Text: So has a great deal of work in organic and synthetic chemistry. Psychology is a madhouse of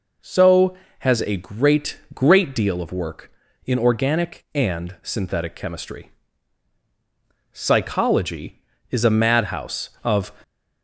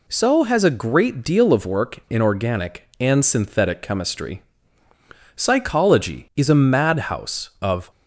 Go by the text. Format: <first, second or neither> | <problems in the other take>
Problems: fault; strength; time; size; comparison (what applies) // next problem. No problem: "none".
second | says "great" twice; at 2.1 s